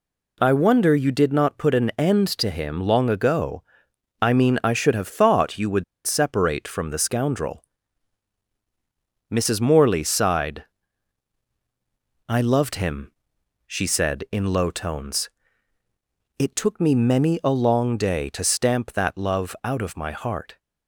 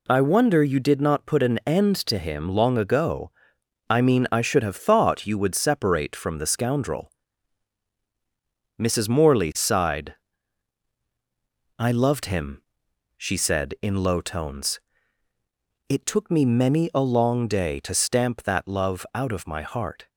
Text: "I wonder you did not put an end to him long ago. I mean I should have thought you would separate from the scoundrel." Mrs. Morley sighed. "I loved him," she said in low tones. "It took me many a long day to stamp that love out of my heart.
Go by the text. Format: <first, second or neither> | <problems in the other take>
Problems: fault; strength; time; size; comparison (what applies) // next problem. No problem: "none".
second | pauses between "would" and "separate"; slight; at 5.8 s; 0.21 s long